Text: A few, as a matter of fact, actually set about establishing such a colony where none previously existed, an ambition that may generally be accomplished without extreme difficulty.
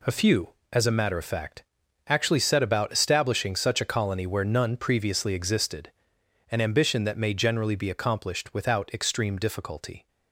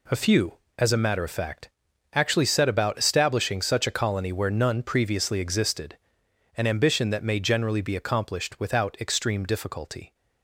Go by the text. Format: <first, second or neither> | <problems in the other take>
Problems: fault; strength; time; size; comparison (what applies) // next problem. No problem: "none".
neither | none